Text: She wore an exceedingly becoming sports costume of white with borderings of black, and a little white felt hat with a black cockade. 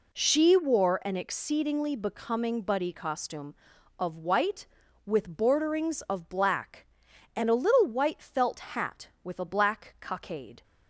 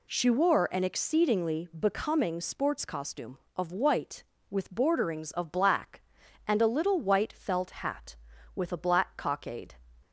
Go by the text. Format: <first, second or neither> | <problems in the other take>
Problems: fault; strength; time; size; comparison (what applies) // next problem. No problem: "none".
second | says "buddy" for "sports"; at 2.6 s